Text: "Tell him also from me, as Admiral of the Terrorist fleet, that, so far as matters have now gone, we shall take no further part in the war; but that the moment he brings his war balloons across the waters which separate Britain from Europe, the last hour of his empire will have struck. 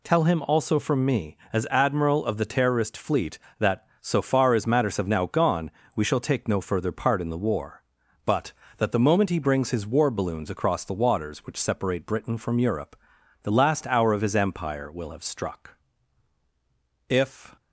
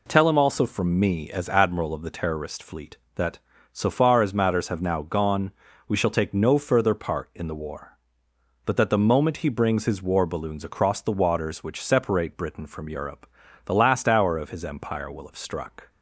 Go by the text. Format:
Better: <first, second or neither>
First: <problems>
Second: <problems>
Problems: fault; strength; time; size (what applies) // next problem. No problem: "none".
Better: second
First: goes on to say "If"; slight; from 17.0 s on; 0.48 s long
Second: none